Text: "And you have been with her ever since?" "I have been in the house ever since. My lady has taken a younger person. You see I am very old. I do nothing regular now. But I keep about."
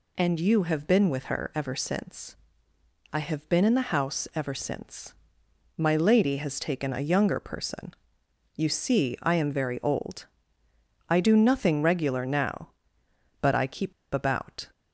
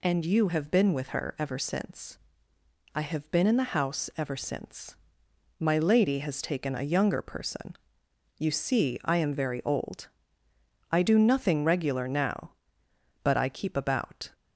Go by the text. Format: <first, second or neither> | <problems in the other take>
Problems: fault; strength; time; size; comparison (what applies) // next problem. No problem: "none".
second | pauses between "keep" and "about"; slight; at 13.9 s; 0.21 s long